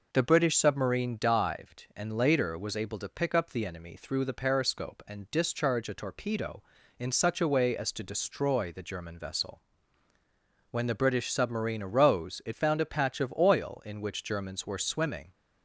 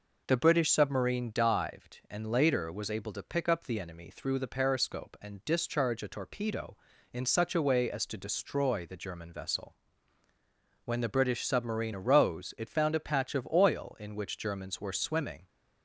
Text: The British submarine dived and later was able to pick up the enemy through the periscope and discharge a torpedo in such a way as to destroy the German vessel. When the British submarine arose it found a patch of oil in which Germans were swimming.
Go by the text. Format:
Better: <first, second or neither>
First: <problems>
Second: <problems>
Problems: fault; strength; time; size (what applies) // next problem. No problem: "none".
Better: neither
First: none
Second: none